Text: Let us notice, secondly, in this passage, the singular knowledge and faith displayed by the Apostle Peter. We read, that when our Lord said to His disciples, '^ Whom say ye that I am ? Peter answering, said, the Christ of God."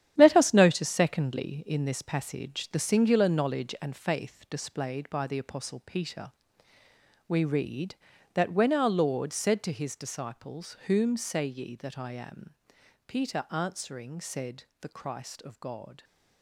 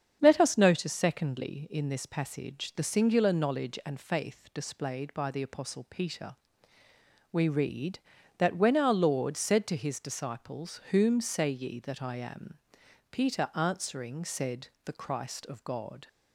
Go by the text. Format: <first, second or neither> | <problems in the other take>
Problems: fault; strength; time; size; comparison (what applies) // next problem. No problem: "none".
second | gets quieter; strong; throughout; 9 dB // starts louder than the rest; strong; until 1.1 s; 10.5 dB; strong in the second